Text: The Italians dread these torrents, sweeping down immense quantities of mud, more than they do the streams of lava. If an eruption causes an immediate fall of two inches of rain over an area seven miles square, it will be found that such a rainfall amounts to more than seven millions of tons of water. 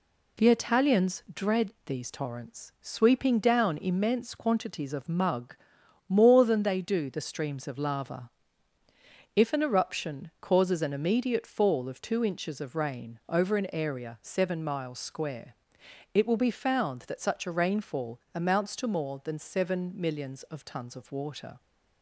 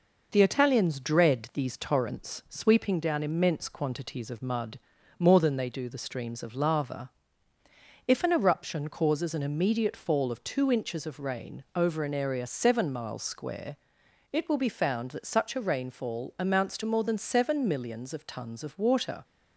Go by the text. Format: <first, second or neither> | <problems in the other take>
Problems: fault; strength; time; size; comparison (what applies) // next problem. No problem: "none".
second | says "mug" for "mud"; at 5.0 s